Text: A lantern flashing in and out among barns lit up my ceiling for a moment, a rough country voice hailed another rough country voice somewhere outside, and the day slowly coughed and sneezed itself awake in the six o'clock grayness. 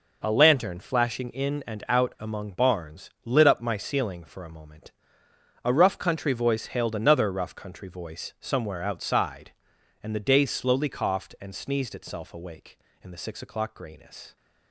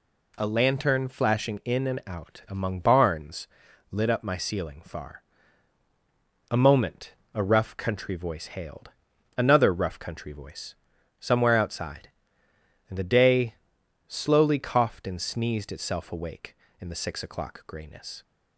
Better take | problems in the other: first | pauses between "barns" and "lit"; noticeable; at 3.4 s; 0.46 s long // says "far" for "for"; at 4.8 s // pauses between "hailed" and "another"; noticeable; at 8.8 s; 0.48 s long // pauses between "voice" and "somewhere"; noticeable; at 10.7 s; 0.46 s long // pauses between "day" and "slowly"; noticeable; at 13.5 s; 0.54 s long

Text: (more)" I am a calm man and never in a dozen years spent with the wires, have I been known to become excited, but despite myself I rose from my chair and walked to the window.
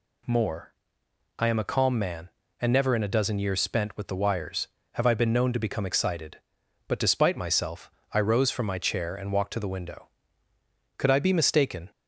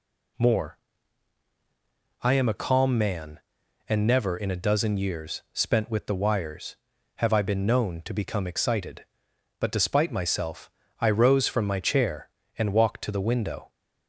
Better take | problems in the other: second | pauses between "myself" and "I"; slight; at 7.9 s; 0.22 s long; slight in the second // goes on to say "Could I be mistaken"; noticeable; from 10.9 s on; 0.94 s long

